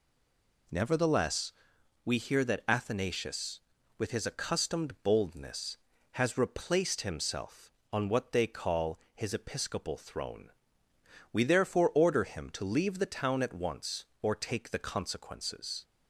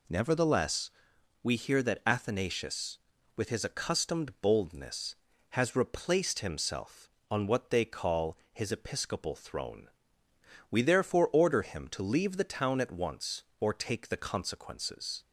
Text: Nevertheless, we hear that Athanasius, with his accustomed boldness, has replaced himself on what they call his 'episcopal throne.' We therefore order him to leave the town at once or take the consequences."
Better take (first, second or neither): second